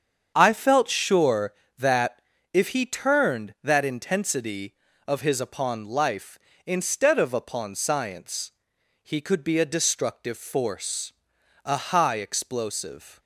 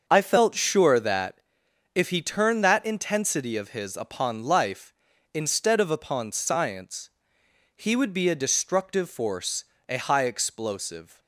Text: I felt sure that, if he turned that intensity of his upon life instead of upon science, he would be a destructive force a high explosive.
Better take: second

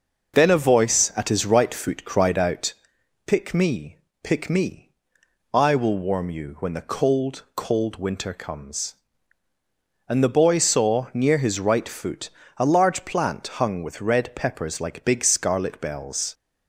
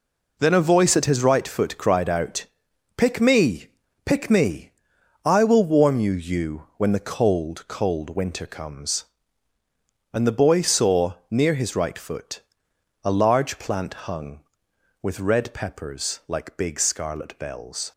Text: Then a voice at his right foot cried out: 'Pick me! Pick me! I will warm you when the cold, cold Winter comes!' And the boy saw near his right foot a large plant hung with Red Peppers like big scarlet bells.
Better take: first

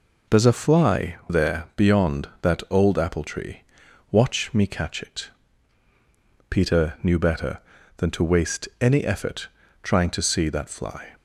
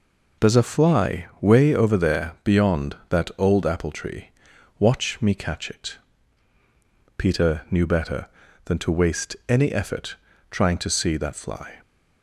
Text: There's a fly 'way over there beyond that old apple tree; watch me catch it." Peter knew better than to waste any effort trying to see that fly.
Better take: second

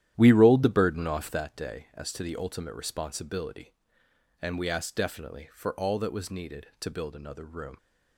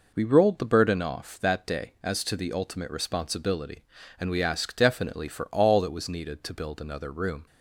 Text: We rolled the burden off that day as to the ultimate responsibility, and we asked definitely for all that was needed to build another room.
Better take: second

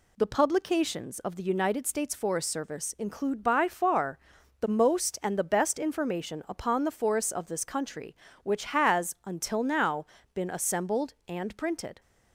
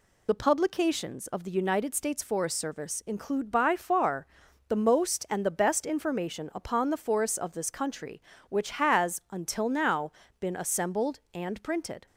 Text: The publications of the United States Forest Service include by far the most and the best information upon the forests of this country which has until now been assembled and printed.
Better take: first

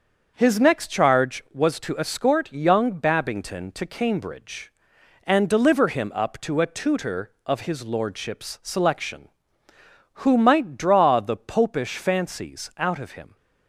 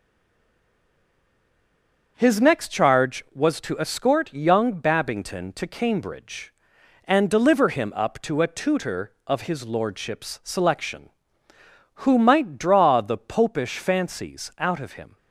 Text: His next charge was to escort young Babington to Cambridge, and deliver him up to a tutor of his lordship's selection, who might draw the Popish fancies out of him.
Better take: first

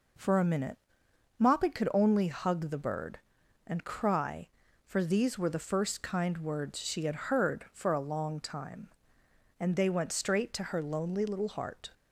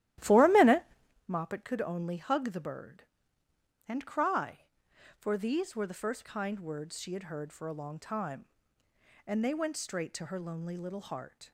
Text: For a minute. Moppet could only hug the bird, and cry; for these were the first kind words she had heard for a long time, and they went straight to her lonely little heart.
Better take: first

